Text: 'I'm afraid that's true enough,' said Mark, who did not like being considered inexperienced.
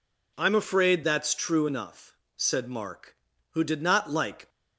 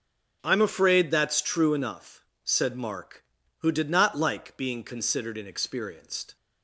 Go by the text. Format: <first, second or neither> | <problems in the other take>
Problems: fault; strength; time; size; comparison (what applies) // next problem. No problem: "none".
second | stops before "being considered inexperienced"; at 4.4 s